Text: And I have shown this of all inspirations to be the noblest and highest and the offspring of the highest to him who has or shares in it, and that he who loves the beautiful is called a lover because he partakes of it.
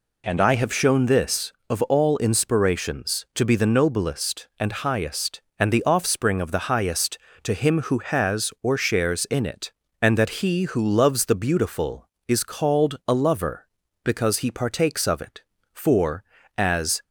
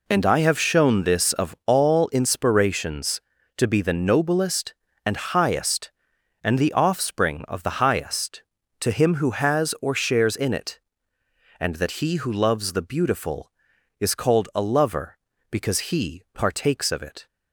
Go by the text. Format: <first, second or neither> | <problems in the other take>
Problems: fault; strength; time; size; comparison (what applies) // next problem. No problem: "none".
second | goes on to say "For as"; noticeable; from 15.7 s on; 1.3 s long